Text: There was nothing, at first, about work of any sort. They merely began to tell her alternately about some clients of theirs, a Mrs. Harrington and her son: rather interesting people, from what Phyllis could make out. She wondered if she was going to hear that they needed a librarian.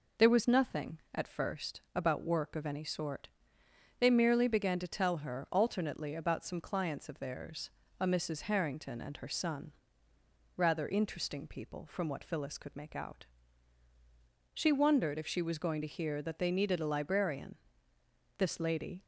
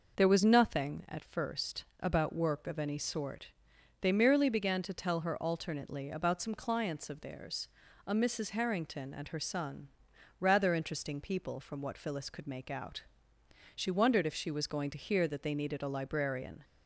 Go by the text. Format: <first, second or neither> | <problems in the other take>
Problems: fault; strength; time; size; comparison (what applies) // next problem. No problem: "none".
second | goes on to say "This lady"; noticeable; from 18.3 s on; 0.68 s long